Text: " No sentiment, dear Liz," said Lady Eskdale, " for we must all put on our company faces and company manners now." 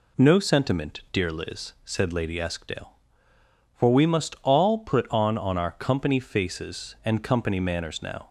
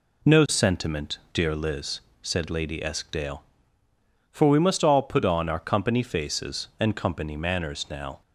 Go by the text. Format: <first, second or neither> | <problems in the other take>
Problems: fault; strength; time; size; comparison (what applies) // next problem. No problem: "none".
second | says "on" twice; at 5.3 s